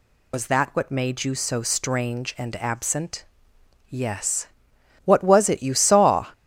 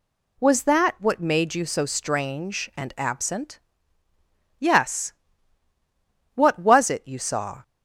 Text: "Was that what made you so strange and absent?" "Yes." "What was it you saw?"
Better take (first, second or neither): second